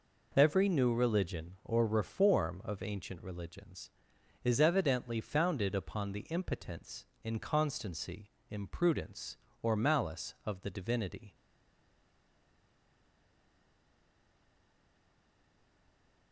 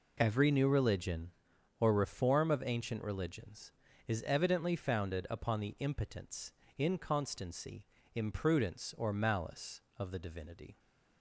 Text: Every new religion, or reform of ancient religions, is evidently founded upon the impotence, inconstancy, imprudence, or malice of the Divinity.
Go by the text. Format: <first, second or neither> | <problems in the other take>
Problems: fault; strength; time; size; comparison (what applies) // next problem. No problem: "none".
second | stays silent after the last word; strong; from 11.3 s on; 5.0 s long